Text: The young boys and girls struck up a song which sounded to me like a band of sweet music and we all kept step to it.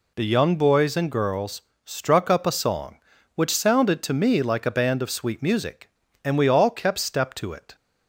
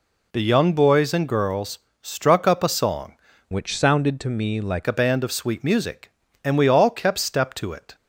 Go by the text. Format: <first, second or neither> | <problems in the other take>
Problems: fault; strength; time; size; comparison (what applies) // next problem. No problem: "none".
first | pauses between "girls" and "struck"; slight; at 1.7 s; 0.24 s long; slight in the first // changes voice from "which" to "like"; from 3.5 to 4.8 s; 1.3 s long